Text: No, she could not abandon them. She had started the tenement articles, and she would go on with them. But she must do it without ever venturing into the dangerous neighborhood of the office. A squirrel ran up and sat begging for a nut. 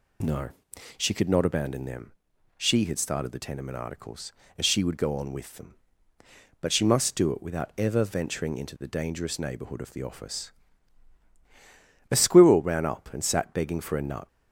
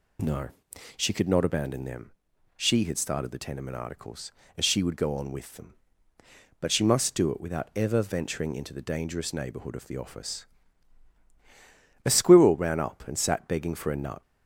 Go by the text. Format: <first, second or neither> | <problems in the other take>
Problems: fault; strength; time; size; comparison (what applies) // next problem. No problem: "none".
neither | none